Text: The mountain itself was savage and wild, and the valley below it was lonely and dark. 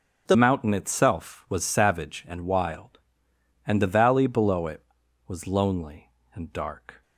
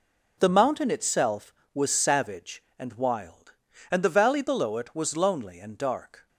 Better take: second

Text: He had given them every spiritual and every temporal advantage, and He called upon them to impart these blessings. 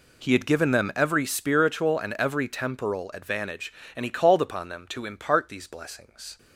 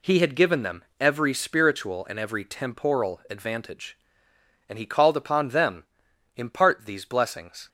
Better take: first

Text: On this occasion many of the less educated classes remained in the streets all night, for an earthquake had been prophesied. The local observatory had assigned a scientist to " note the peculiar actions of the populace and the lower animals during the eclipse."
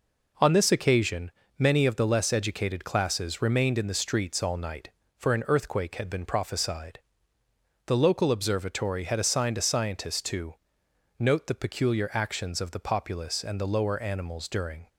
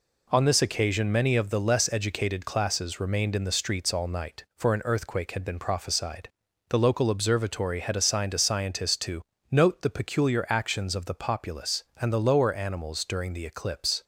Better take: second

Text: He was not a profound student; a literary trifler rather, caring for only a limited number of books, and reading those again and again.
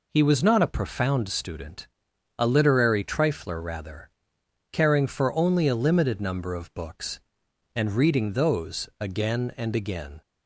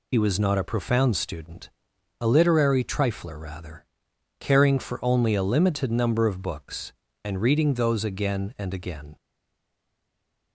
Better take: first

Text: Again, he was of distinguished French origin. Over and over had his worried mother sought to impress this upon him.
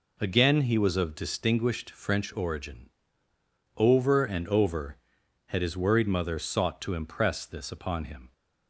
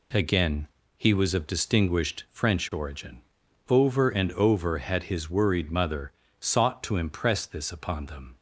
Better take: first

